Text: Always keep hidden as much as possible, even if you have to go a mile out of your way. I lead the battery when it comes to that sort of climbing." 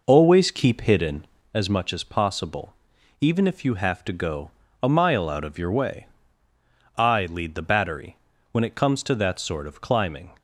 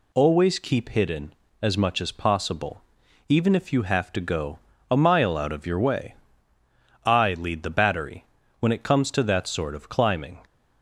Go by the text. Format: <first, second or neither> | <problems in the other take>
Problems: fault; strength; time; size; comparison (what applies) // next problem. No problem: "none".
second | starts louder than the rest; noticeable; until 1.6 s; 5 dB // pauses between "go" and "a"; slight; at 4.5 s; 0.32 s long; slight in the second // pauses between "battery" and "when"; slight; at 8.1 s; 0.34 s long; slight in the second